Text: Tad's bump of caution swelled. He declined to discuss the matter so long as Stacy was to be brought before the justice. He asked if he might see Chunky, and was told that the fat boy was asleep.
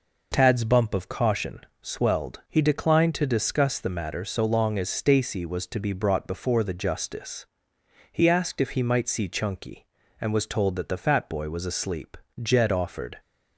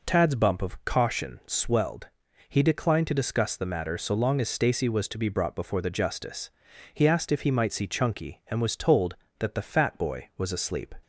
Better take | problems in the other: second | pauses between "caution" and "swelled"; slight; at 1.6 s; 0.22 s long // goes on to say "Jed offered"; noticeable; from 12.4 s on; 0.78 s long

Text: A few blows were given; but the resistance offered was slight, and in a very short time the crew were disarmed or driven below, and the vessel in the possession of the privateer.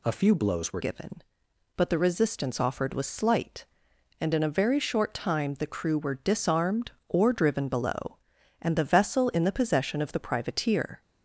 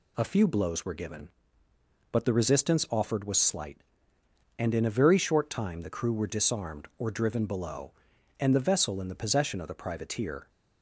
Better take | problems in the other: second | changes voice at "given"; from 0.7 s on; 10.3 s long

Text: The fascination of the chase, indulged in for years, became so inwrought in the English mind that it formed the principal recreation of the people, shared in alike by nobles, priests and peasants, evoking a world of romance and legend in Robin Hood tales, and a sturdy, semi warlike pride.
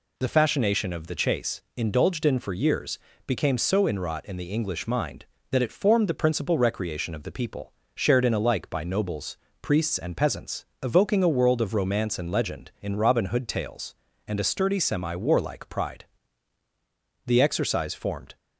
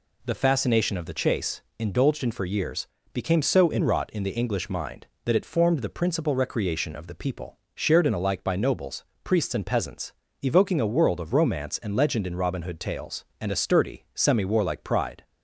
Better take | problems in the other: second | goes on to say "The exercise formed"; noticeable; from 17.2 s on; 1.1 s long

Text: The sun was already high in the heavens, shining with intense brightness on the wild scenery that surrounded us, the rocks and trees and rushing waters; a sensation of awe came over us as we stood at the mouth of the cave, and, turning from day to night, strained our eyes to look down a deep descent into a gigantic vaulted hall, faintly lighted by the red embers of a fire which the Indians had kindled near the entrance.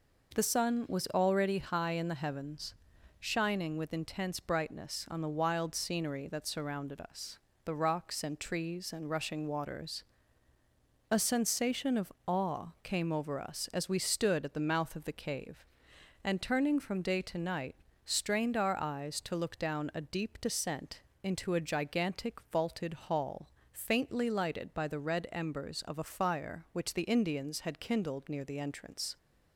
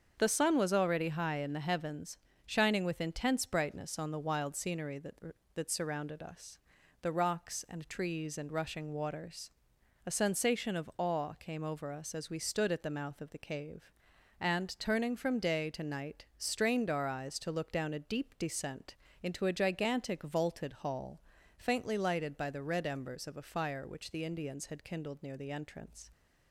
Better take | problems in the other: first | starts louder than the rest; until 1.1 s; 7 dB // says "that" twice; at 5.5 s // pauses between "descent" and "into"; slight; at 18.9 s; 0.28 s long; slight in the first

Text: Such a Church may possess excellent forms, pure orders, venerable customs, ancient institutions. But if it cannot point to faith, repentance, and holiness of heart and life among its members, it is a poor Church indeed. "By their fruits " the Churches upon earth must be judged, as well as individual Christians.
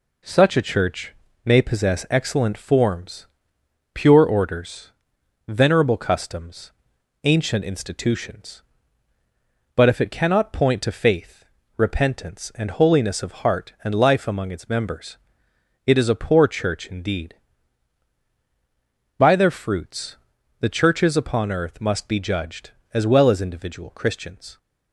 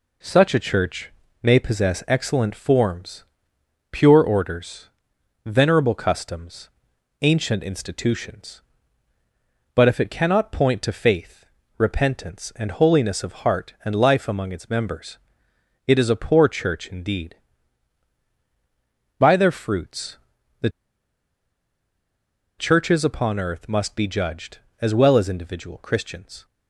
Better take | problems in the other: first | pauses between "Church" and "may"; slight; at 1.1 s; 0.32 s long; slight in the first // pauses between "the" and "Churches"; strong; at 20.7 s; 1.8 s long

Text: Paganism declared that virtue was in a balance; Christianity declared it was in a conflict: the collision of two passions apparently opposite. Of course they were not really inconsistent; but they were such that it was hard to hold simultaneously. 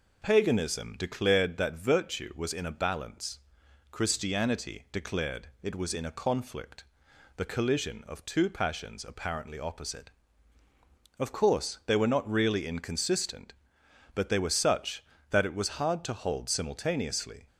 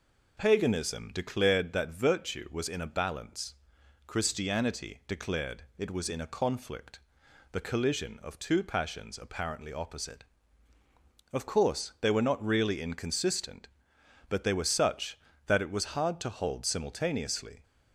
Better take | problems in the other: neither | none

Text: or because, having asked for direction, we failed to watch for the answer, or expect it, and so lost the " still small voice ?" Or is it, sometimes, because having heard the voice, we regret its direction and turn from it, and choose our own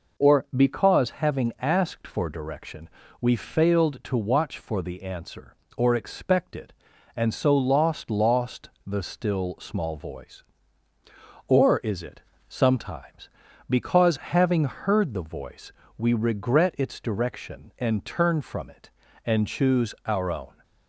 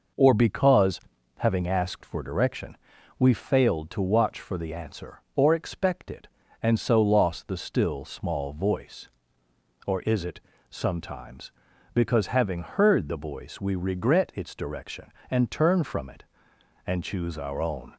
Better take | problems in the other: second | says "lost" twice; at 8.0 s

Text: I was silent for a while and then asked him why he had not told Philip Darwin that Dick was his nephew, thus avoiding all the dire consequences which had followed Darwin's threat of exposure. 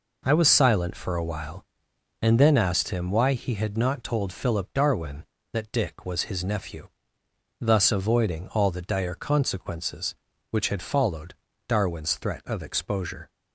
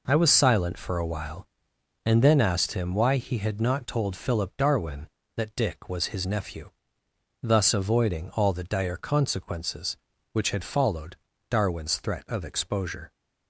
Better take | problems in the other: neither | pauses between "followed" and "Darwin's"; slight; the same in both

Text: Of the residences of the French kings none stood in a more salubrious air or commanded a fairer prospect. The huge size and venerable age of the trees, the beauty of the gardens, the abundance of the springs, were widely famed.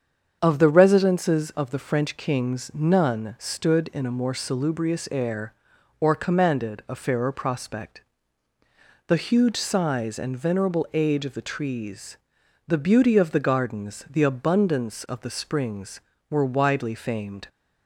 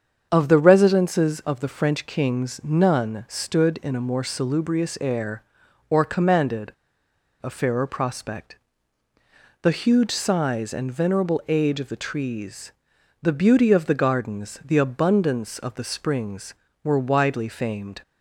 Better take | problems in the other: first | starts louder than the rest; strong; until 1.3 s; 7.5 dB; strong in the first // pauses between "commanded" and "a"; noticeable; at 6.7 s; 0.71 s long

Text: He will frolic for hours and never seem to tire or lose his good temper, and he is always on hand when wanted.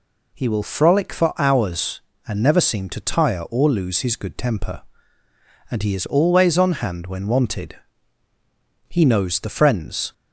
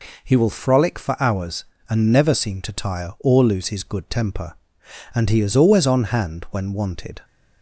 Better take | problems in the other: second | goes on to say "He knows the friends"; noticeable; from 8.8 s on; 1.2 s long

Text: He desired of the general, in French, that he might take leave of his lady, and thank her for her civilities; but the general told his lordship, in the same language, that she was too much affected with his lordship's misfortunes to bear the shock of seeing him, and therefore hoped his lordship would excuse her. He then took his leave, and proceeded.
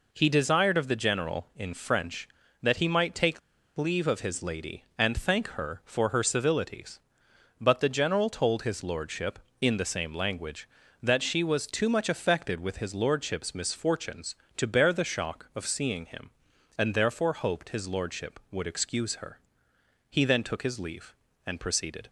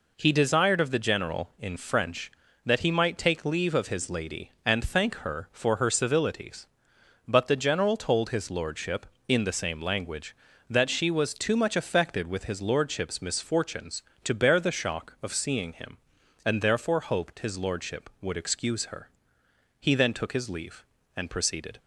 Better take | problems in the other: second | pauses between "take" and "leave"; at 3.4 s; 0.38 s long

